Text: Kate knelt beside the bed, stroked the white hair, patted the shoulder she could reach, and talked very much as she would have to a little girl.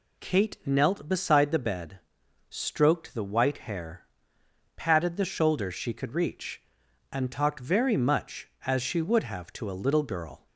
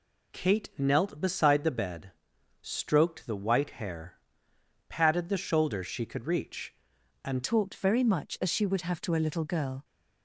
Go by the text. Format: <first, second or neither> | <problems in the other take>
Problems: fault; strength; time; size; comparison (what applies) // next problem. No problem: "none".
first | changes voice at "talked"; from 7.4 s on; 2.4 s long